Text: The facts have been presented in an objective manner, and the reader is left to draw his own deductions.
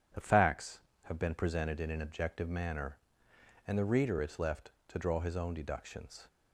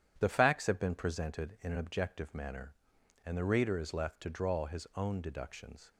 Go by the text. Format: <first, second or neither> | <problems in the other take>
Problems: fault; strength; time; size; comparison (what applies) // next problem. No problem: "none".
neither | starts louder than the rest; strong; the same in both